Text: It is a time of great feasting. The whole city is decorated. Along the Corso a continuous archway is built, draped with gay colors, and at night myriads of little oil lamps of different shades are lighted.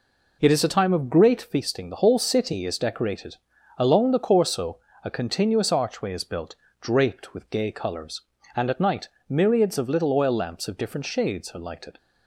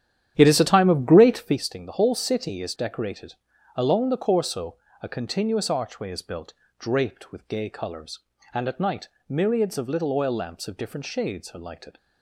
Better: first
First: pauses between "Corso" and "a"; slight; at 4.7 s; 0.24 s long // pauses between "night" and "myriads"; slight; at 9.0 s; 0.20 s long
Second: starts louder than the rest; strong; until 1.7 s; 10.5 dB // pauses between "Corso" and "a"; slight; at 4.7 s; 0.24 s long // pauses between "night" and "myriads"; slight; at 9.0 s; 0.20 s long

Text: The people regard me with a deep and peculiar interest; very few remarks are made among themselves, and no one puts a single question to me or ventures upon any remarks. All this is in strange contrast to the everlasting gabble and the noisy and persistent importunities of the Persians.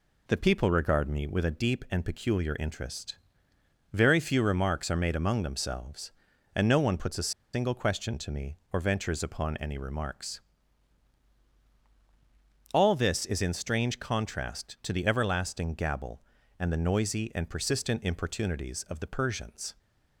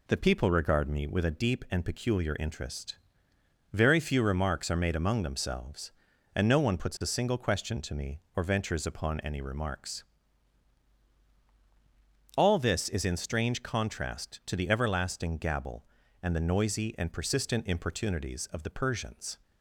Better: second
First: pauses between "a" and "single"; slight; at 7.3 s; 0.23 s long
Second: none

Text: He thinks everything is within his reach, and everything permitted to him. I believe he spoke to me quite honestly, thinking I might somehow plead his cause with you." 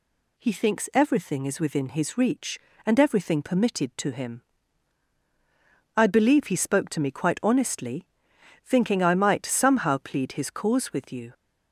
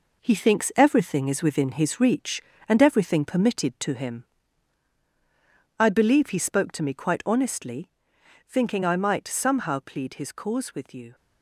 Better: first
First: none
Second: gets quieter; strong; throughout; 7 dB

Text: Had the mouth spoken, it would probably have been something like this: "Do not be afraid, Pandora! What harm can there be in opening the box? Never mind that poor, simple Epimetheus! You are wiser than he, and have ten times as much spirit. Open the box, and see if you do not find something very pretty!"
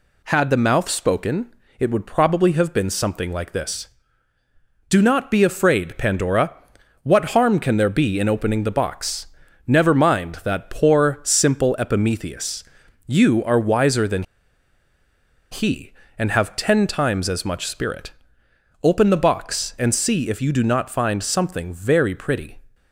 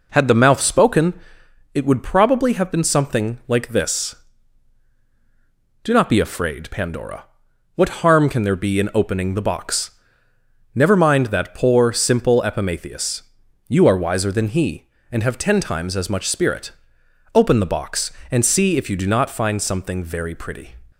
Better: second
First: pauses between "than" and "he"; strong; at 14.2 s; 1.2 s long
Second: none

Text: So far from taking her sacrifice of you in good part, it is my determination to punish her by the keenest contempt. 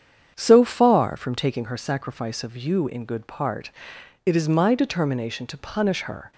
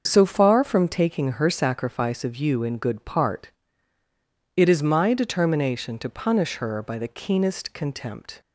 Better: second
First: starts louder than the rest; strong; until 1.3 s; 7.5 dB // stops before "by the keenest contempt"; at 6.3 s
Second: starts louder than the rest; until 1.0 s; 6.5 dB

